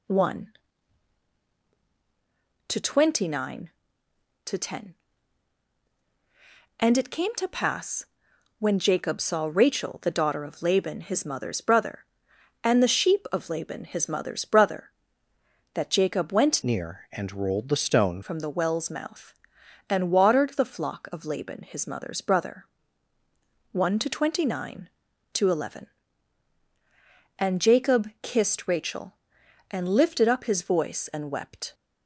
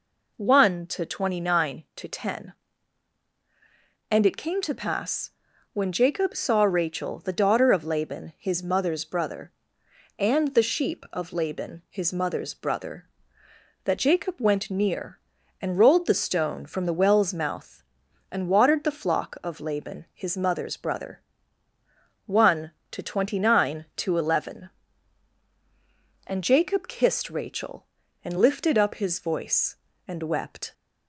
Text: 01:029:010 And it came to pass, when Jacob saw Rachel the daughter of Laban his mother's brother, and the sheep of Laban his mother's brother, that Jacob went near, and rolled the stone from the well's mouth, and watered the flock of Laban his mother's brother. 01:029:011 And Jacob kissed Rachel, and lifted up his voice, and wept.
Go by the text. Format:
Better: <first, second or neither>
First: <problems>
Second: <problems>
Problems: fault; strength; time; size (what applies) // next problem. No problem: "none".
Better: second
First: changes voice from "near" to "stone"; from 16.6 to 18.2 s; 1.6 s long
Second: none